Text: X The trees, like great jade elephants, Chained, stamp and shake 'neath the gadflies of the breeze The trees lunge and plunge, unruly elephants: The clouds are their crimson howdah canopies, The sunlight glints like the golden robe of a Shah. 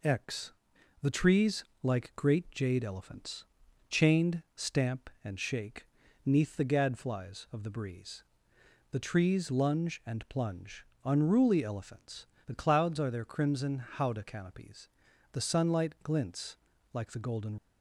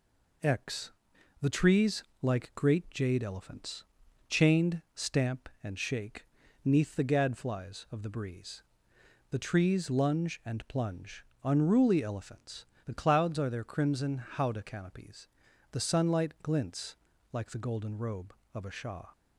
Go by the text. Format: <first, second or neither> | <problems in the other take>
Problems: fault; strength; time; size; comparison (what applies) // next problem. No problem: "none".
second | pauses between "X" and "The"; noticeable; at 0.5 s; 0.50 s long; noticeable in the second // pauses between "shake" and "neath"; at 5.8 s; 0.38 s long; also in the second // pauses between "breeze" and "The"; noticeable; at 8.2 s; 0.70 s long; noticeable in the second // pauses between "glints" and "like"; slight; at 16.5 s; 0.36 s long; slight in the second // stops before "robe of a Shah"; at 17.5 s